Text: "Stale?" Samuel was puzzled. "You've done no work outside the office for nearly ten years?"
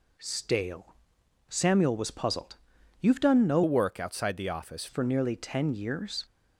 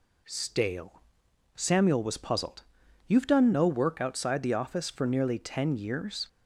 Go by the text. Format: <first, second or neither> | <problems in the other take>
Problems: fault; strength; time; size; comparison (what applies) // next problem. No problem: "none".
second | changes voice from "work" to "office"; from 3.6 to 4.8 s; 1.2 s long